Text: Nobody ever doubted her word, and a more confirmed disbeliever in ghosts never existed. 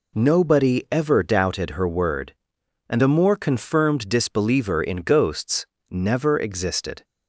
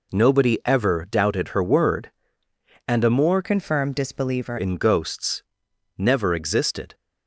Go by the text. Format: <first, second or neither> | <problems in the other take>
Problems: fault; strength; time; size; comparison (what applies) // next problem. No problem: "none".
first | changes voice from "confirmed" to "disbeliever"; from 3.4 to 4.5 s; 1.1 s long // pauses between "ghosts" and "never"; noticeable; at 5.4 s; 0.56 s long; slight in the first